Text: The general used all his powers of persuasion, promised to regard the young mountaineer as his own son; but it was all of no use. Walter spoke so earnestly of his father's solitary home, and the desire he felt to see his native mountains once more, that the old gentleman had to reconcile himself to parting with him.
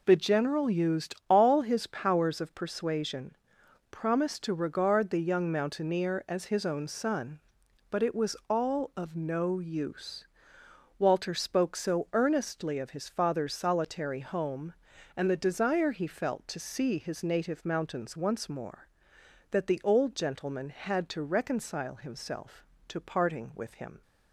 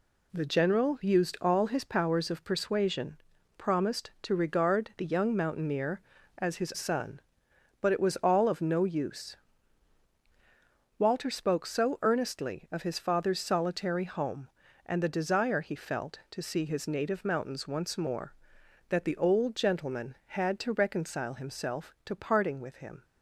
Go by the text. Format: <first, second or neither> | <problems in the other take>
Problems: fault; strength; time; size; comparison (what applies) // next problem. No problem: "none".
first | skips "own"; at 6.7 s